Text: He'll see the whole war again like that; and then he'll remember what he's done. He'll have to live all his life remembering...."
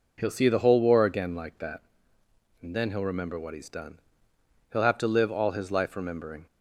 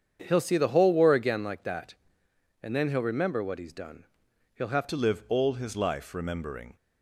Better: first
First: none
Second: starts louder than the rest; strong; until 1.2 s; 8 dB // changes voice at "to"; from 4.8 s on; 1.9 s long

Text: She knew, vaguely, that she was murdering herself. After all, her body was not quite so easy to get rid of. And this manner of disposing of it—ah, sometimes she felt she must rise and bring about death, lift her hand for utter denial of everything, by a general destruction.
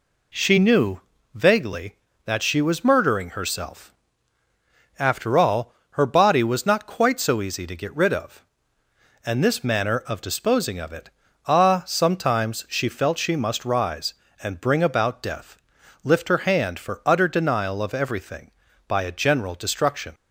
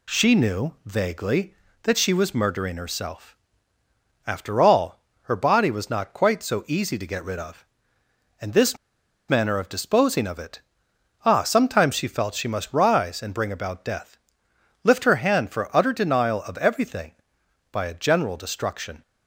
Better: first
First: none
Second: pauses between "this" and "manner"; noticeable; at 8.7 s; 0.53 s long

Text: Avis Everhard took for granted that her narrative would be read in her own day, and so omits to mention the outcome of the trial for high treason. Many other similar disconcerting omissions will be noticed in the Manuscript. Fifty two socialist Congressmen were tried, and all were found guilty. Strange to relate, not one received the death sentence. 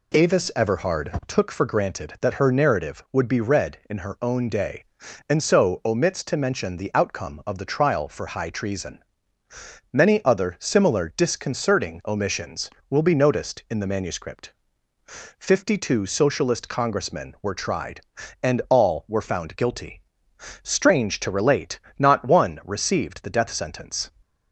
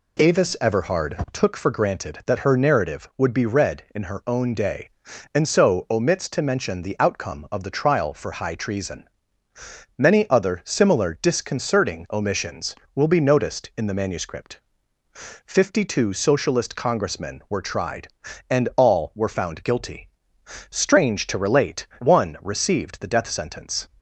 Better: first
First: none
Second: skips "not"; at 21.9 s

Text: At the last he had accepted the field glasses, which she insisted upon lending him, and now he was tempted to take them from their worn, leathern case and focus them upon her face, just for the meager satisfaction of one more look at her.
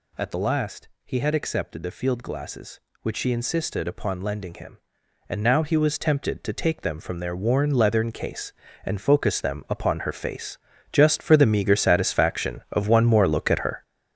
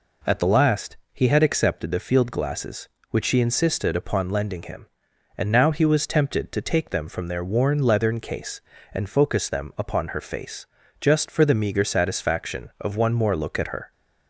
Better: second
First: gets louder; strong; throughout; 9 dB // pauses between "last" and "he"; slight; at 0.8 s; 0.16 s long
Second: pauses between "last" and "he"; slight; at 0.9 s; 0.16 s long

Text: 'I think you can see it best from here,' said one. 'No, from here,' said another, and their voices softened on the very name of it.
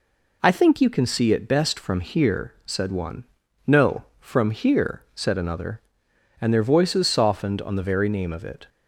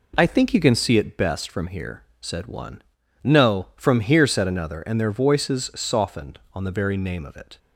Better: neither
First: none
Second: none

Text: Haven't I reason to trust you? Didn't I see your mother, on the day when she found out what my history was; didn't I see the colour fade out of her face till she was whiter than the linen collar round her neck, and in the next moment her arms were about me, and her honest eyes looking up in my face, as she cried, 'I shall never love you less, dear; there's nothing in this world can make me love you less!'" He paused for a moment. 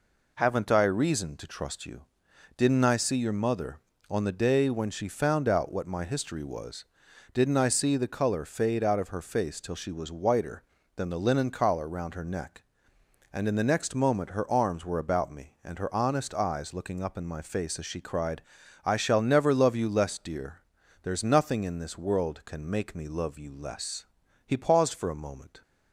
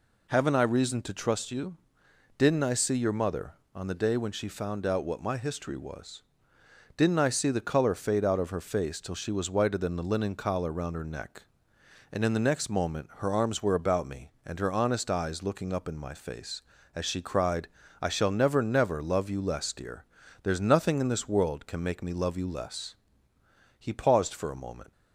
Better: first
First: none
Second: says "never" twice; at 18.6 s

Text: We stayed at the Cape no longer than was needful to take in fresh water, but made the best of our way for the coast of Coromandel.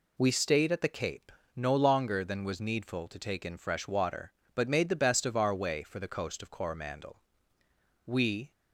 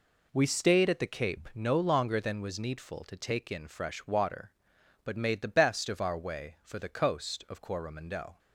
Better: second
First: pauses between "Cape" and "no"; slight; at 1.3 s; 0.24 s long // goes on to say "We"; slight; from 8.0 s on; 0.46 s long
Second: none

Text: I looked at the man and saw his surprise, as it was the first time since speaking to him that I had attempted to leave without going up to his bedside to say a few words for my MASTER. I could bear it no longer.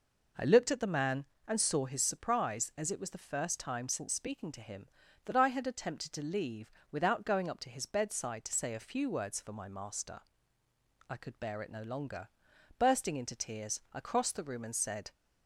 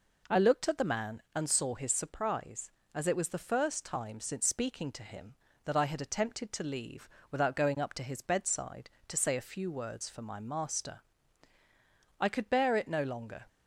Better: second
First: pauses between "leave" and "without"; slight; at 6.7 s; 0.20 s long // goes on to say "Bursting into tears I crossed the room and said"; strong; from 12.7 s on; 2.3 s long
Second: pauses between "leave" and "without"; slight; at 7.0 s; 0.22 s long

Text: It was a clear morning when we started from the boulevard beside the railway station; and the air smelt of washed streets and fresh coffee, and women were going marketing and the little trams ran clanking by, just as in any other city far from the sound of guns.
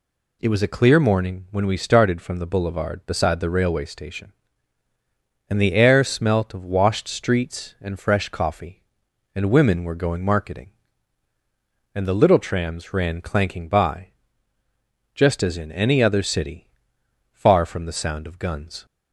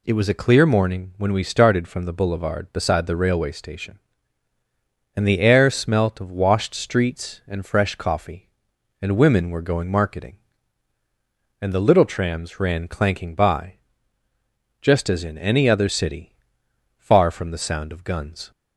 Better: neither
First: pauses between "city" and "far"; noticeable; at 16.6 s; 0.64 s long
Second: pauses between "city" and "far"; noticeable; at 16.3 s; 0.64 s long

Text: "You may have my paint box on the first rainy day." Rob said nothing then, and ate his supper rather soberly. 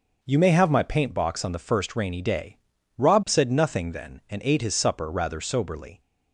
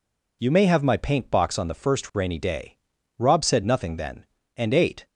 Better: first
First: none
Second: stops before "his supper rather soberly"; at 5.0 s

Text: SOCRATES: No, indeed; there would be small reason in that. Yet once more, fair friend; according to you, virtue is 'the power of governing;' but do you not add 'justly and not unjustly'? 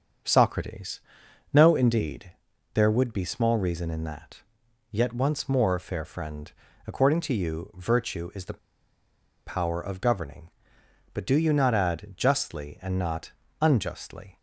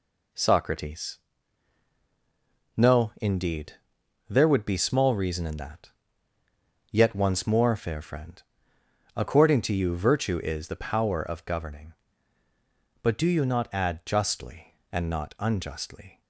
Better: second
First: starts louder than the rest; until 1.7 s; 6.5 dB // pauses between "the" and "power"; noticeable; at 8.5 s; 0.90 s long // pauses between "not" and "unjustly"; slight; at 13.3 s; 0.28 s long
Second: none

